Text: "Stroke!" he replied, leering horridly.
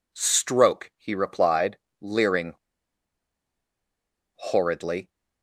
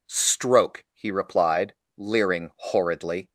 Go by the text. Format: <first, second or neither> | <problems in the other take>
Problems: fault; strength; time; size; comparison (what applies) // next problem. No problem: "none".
second | pauses between "leering" and "horridly"; strong; at 2.5 s; 1.8 s long